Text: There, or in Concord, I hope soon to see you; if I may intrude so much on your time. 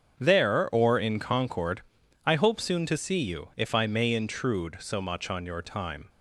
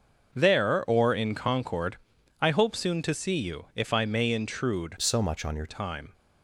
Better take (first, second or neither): first